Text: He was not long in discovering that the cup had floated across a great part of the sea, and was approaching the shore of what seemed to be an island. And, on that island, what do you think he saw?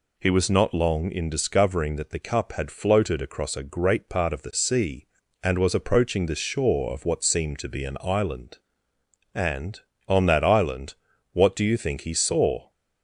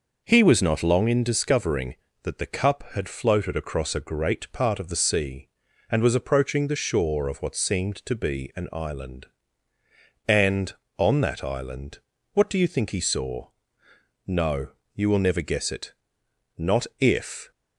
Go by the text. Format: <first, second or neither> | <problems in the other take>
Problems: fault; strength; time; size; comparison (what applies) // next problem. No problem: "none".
first | goes on to say "No you will never guess it not if"; strong; from 14.2 s on; 3.2 s long